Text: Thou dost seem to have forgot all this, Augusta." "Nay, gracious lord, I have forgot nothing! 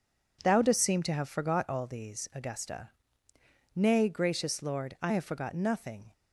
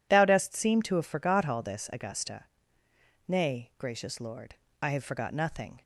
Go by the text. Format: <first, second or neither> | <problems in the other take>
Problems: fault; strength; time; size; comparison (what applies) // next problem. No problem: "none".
second | says "these" for "this"; at 1.8 s